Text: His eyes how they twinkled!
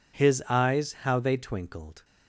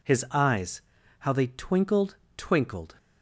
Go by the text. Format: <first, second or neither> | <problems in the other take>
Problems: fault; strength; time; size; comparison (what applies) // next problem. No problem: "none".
first | pauses between "eyes" and "how"; at 0.8 s; 0.38 s long // says "twinkled" twice; at 2.3 s